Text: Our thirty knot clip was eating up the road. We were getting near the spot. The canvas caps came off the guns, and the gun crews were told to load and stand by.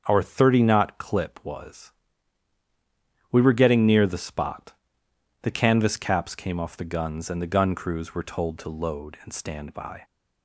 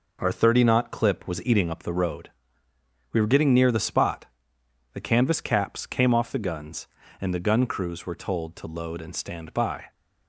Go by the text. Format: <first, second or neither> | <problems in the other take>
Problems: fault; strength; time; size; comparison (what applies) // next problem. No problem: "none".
second | starts louder than the rest; until 1.0 s; 7 dB // skips "eating up the road"; at 2.6 s